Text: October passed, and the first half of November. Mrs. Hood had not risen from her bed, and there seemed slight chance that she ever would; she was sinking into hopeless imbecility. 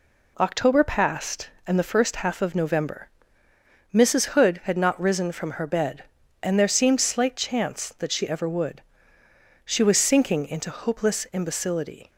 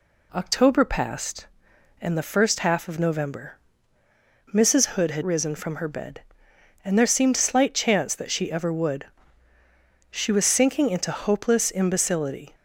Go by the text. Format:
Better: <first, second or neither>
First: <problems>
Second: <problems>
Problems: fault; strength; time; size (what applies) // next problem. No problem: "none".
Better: first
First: none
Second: skips "not"; at 5.2 s